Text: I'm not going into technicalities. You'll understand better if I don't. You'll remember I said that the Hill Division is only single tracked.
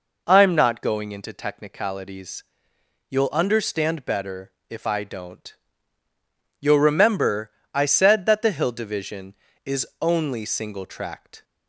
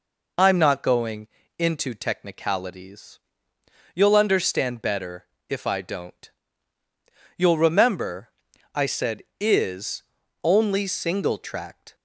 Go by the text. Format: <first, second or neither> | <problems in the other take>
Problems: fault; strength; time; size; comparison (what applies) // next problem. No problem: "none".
first | pauses between "going" and "into"; slight; at 1.2 s; 0.30 s long // pauses between "better" and "if"; slight; at 5.2 s; 0.24 s long; slight in the first // pauses between "remember" and "I"; at 8.2 s; 0.44 s long; slight in the first // skips "that the Hill Division"; at 9.3 s // pauses between "is" and "only"; at 10.0 s; 0.40 s long